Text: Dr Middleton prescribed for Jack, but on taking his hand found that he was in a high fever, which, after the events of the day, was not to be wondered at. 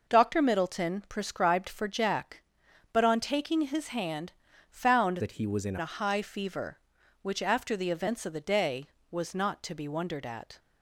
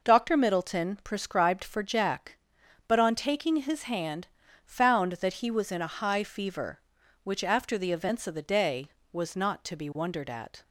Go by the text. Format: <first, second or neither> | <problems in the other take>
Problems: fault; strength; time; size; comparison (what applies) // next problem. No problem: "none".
second | pauses between "hand" and "found"; slight; at 4.3 s; 0.36 s long; slight in the second // changes voice from "that" to "in"; from 5.2 to 5.7 s; 0.5 s long